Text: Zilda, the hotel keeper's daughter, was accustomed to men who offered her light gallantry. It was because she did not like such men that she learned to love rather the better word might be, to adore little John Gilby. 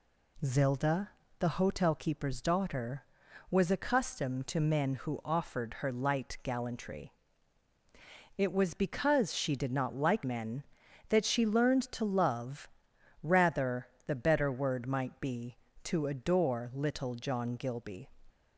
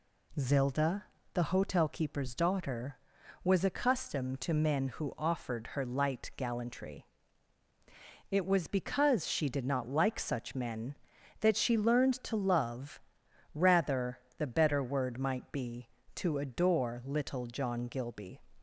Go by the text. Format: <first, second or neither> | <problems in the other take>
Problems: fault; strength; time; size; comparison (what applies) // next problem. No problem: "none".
second | skips "such"; at 10.2 s // pauses between "love" and "rather"; noticeable; at 12.6 s; 0.54 s long; noticeable in the second // pauses between "rather" and "the"; slight; at 13.8 s; 0.20 s long; slight in the second